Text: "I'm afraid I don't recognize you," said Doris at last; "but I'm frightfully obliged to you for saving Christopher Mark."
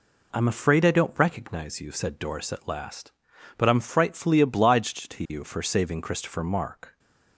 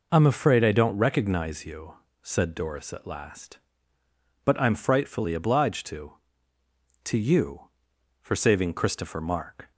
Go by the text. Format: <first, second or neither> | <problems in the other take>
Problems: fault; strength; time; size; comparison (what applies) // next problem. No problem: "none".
first | says "to" twice; at 7.0 s